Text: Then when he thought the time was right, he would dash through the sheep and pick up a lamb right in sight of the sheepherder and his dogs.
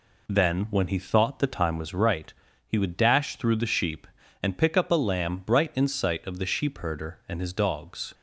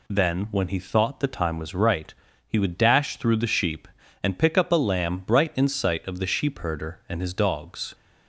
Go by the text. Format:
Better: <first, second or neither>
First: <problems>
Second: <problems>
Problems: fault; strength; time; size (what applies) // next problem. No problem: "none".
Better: second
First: starts louder than the rest; slight; until 2.1 s; 3 dB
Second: none